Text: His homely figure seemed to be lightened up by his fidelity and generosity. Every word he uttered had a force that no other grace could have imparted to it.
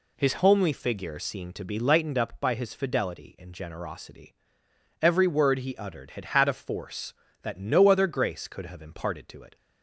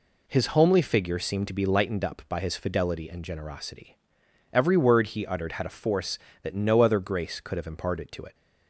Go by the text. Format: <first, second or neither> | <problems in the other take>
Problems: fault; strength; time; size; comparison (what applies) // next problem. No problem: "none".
second | says "had" twice; at 6.2 s